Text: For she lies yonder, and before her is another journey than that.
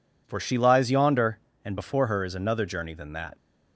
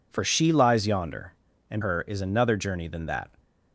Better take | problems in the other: first | skips "before"; at 1.8 s

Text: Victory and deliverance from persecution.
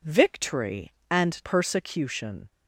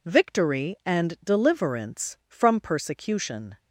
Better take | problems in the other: second | skips "deliverance from"; at 1.4 s

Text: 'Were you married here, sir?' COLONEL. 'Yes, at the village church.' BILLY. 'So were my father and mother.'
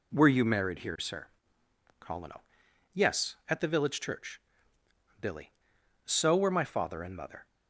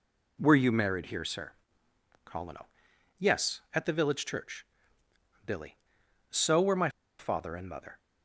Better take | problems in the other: first | pauses between "my" and "father"; slight; at 6.8 s; 0.30 s long

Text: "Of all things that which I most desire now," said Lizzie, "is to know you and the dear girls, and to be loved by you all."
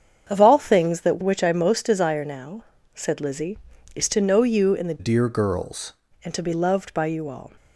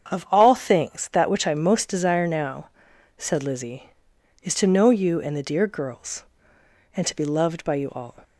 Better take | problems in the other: second | starts louder than the rest; strong; until 1.3 s; 7.5 dB; strong in the second // changes voice from "dear" to "girls"; from 4.9 to 5.9 s; 1.0 s long

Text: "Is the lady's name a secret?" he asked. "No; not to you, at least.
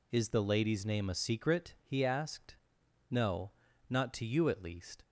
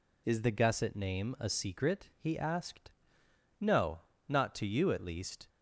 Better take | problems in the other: first | says "gusset" for "lady's"; at 0.5 s

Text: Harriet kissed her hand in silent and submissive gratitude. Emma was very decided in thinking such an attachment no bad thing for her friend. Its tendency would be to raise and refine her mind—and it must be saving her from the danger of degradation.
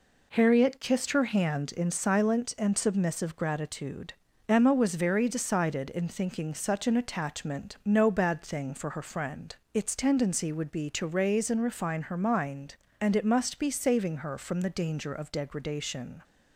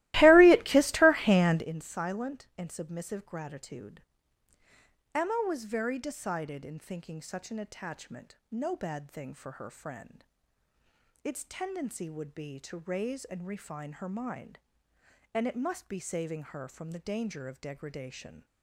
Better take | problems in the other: first | starts louder than the rest; strong; until 1.7 s; 18 dB

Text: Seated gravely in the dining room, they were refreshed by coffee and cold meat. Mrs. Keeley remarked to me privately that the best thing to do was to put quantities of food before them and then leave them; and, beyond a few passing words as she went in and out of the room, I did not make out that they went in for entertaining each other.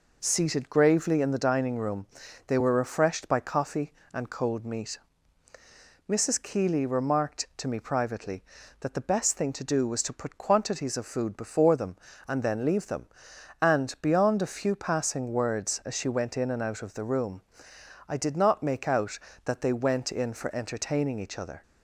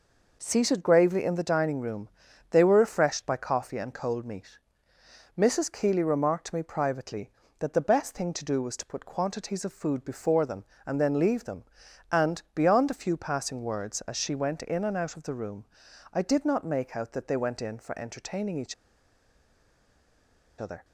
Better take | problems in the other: first | pauses between "each" and "other"; strong; at 18.7 s; 1.8 s long

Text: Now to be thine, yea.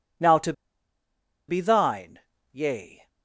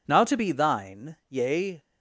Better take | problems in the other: second | pauses between "to" and "be"; noticeable; at 0.5 s; 0.96 s long

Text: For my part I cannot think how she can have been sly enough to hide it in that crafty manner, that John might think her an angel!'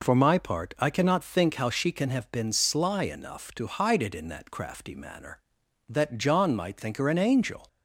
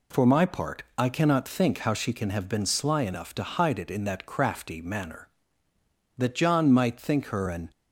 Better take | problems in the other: first | stops before "angel"; at 7.7 s

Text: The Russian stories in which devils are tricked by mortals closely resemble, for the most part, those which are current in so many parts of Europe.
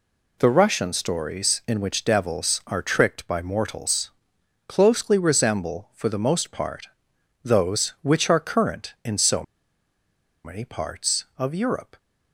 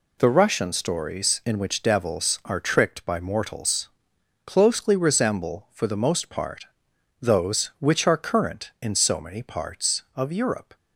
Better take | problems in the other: second | pauses between "mortals" and "closely"; noticeable; at 4.1 s; 0.58 s long; noticeable in the second // pauses between "so" and "many"; at 9.4 s; 1.0 s long

